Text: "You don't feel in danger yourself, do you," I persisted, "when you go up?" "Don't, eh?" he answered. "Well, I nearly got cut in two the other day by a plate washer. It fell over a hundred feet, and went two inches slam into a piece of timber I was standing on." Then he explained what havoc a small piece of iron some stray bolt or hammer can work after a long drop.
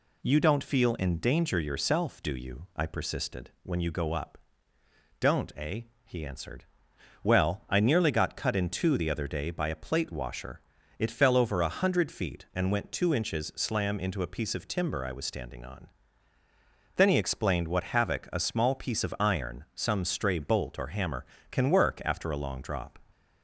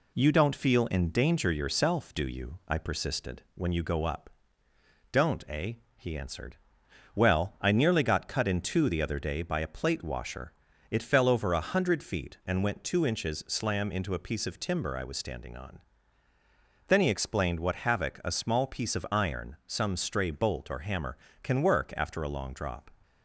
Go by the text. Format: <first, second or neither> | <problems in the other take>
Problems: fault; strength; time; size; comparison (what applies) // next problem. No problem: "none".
first | gets quieter; slight; throughout; 2 dB